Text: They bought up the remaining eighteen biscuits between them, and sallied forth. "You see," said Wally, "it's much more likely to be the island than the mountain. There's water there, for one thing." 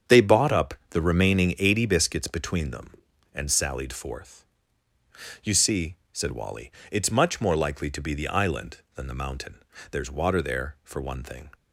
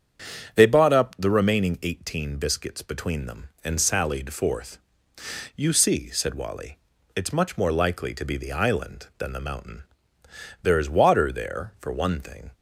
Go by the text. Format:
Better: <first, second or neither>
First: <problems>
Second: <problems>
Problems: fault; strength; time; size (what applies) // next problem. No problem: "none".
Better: second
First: starts louder than the rest; strong; until 1.2 s; 7.5 dB // pauses between "up" and "the"; slight; at 0.7 s; 0.18 s long // says "eighty" for "eighteen"; at 1.5 s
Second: starts louder than the rest; strong; until 1.5 s; 7.5 dB